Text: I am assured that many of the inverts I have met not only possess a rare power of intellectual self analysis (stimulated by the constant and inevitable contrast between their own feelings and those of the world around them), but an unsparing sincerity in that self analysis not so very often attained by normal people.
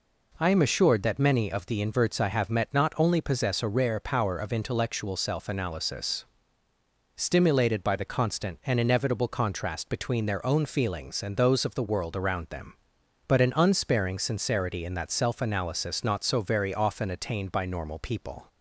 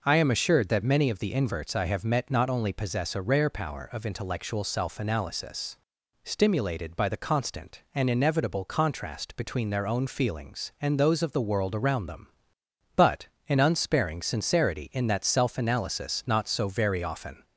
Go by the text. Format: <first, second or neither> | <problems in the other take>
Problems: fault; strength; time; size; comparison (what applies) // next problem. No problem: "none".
first | pauses between "but" and "an"; slight; at 13.2 s; 0.20 s long // stops before "attained by normal people"; at 17.4 s